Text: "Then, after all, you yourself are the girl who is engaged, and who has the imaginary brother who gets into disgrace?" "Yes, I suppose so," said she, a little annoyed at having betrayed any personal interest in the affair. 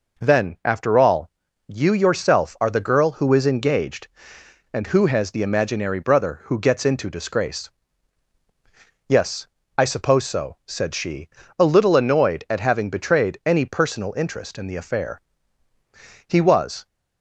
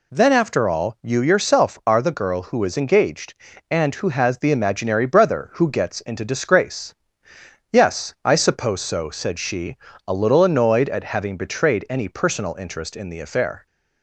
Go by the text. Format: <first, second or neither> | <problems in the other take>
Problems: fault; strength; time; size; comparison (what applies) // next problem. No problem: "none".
second | goes on to say "He was"; from 16.2 s on; 0.60 s long